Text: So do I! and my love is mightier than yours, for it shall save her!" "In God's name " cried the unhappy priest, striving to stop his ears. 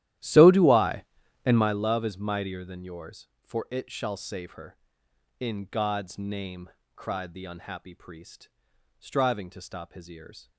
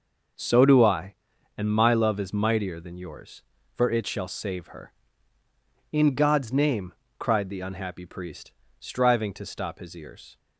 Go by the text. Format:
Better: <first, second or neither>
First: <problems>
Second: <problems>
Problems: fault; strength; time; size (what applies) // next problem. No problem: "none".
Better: second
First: starts louder than the rest; strong; until 1.8 s; 13 dB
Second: none